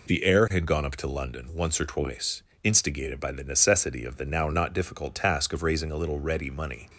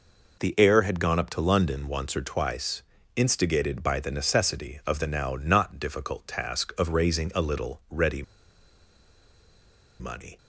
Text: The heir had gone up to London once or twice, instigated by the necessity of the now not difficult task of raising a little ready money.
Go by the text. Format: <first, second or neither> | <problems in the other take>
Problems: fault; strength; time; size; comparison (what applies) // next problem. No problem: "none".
first | pauses between "ready" and "money"; strong; at 8.2 s; 1.7 s long